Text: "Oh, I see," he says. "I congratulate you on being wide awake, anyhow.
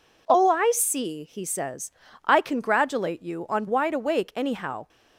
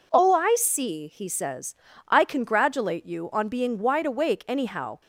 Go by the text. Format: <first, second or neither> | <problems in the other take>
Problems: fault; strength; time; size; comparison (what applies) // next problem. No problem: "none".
second | skips "being"; at 3.6 s